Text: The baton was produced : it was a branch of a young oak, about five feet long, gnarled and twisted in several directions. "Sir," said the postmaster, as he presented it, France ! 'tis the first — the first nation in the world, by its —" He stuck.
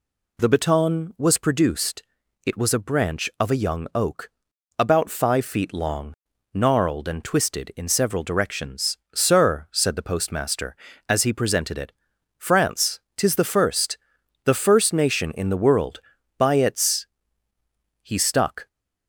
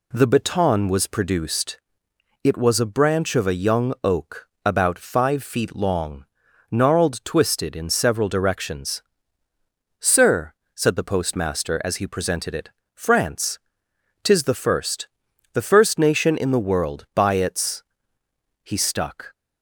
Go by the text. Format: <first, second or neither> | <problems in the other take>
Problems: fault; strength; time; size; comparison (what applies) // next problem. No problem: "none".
first | skips "and"; at 7.2 s